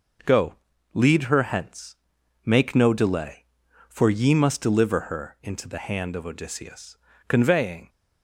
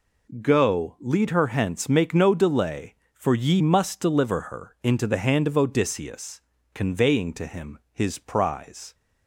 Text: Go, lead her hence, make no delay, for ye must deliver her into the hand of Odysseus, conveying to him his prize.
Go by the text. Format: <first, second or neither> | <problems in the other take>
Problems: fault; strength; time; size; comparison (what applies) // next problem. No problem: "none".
second | stops before "to him his prize"; at 7.8 s